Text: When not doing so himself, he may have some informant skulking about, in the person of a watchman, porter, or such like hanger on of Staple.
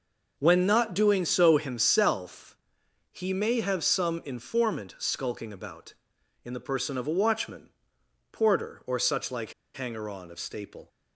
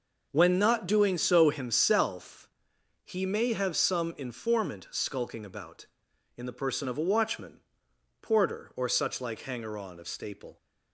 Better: second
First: pauses between "like" and "hanger"; slight; at 9.5 s; 0.21 s long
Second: none

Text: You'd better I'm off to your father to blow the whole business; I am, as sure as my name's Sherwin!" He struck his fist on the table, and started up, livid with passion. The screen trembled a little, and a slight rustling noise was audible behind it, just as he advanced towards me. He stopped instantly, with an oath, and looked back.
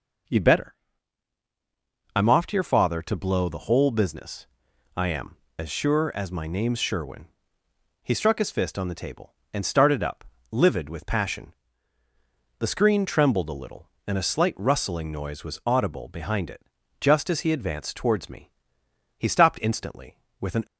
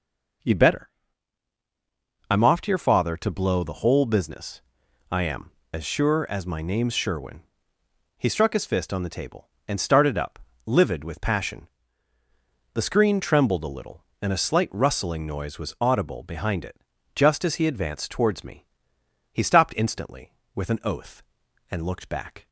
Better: second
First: pauses between "better" and "I'm"; strong; at 0.7 s; 1.4 s long // stops before "oath and looked back"; at 20.6 s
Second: pauses between "better" and "I'm"; strong; at 0.8 s; 1.4 s long

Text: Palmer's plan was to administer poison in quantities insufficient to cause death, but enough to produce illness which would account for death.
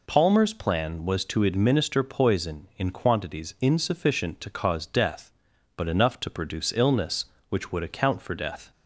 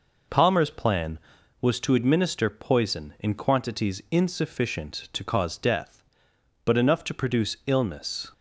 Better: first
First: none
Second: stops before "which would account for death"; at 8.3 s

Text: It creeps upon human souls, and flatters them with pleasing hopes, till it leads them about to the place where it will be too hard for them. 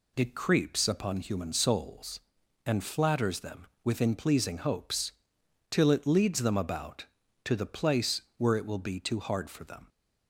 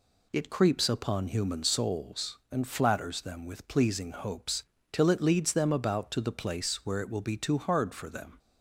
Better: second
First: says "within" for "with"; at 3.8 s // pauses between "place" and "where"; slight; at 8.2 s; 0.16 s long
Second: none

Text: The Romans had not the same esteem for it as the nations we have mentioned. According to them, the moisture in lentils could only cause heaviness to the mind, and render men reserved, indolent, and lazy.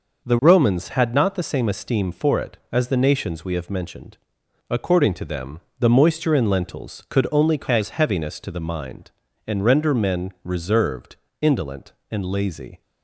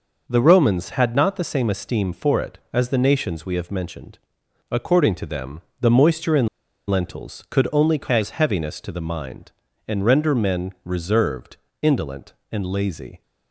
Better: first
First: none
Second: pauses between "in" and "lentils"; at 6.4 s; 0.41 s long

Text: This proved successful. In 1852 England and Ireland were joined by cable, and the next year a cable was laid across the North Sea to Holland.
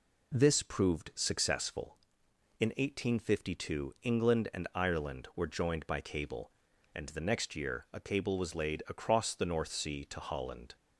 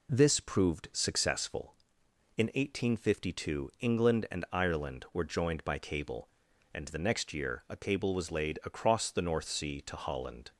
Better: neither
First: none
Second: none

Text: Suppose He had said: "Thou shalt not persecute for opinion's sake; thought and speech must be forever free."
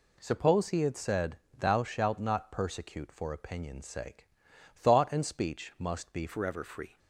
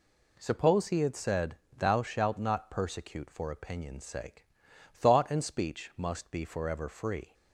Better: second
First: changes voice at "forever"; from 6.2 s on; 0.7 s long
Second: none

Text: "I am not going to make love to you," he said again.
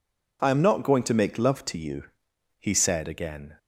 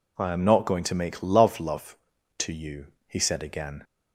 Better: first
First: none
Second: says "love" twice; at 1.5 s

